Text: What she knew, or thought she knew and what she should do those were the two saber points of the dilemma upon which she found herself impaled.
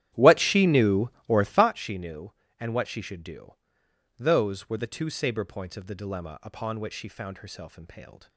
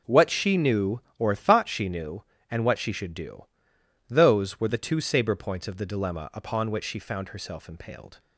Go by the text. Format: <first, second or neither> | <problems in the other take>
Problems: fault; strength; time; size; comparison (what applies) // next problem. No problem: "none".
second | starts louder than the rest; strong; until 1.7 s; 12 dB // pauses between "do" and "those"; noticeable; at 3.5 s; 0.64 s long; noticeable in the second